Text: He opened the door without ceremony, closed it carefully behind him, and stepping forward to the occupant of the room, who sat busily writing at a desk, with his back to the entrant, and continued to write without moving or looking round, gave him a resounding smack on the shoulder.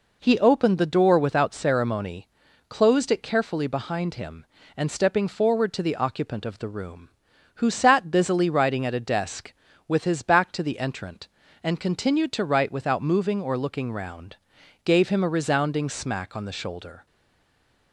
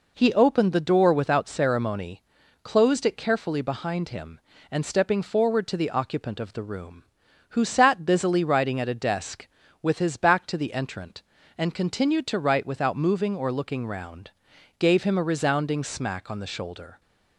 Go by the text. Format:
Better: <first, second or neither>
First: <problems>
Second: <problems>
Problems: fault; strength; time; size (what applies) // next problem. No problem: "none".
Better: second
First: stays silent after the last word; slight; from 17.0 s on; 0.9 s long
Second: none